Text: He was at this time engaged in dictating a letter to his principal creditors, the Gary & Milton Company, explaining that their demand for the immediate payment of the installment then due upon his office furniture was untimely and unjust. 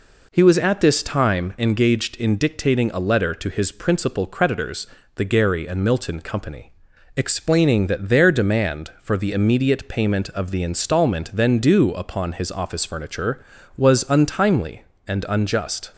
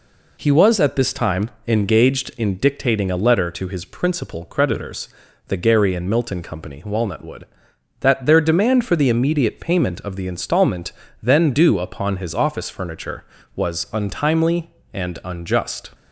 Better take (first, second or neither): first